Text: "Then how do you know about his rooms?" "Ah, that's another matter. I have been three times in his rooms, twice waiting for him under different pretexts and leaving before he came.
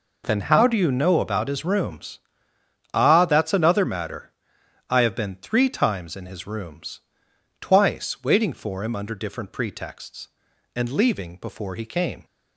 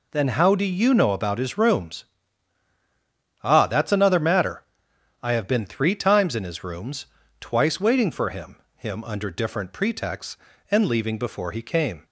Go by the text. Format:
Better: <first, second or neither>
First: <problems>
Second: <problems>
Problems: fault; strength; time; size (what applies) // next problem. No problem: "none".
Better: first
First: none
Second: says "him" twice; at 8.7 s